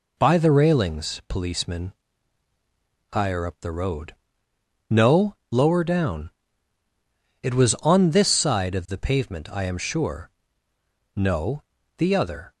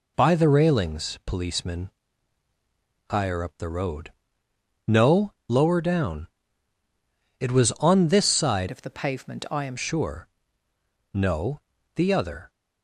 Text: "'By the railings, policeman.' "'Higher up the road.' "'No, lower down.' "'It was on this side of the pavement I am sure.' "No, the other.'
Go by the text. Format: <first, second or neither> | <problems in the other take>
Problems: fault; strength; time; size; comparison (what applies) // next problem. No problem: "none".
first | changes voice from "of" to "am"; from 8.6 to 9.7 s; 1.1 s long